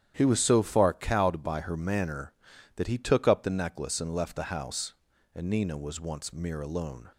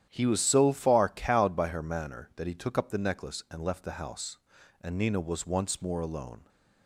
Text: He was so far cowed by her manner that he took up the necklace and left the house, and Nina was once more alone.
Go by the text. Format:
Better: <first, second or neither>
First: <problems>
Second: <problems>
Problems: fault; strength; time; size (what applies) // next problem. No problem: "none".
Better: second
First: starts louder than the rest; strong; until 1.1 s; 10 dB // says "mere" for "more"; at 6.3 s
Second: starts louder than the rest; strong; until 1.1 s; 10.5 dB